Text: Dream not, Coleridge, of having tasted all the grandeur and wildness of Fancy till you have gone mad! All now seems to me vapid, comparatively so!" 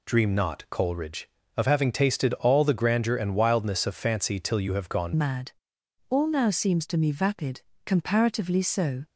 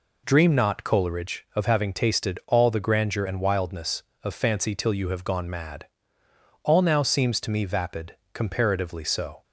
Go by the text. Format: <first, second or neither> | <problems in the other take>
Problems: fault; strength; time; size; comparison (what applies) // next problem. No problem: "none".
second | changes voice at "mad"; from 5.1 s on; 3.9 s long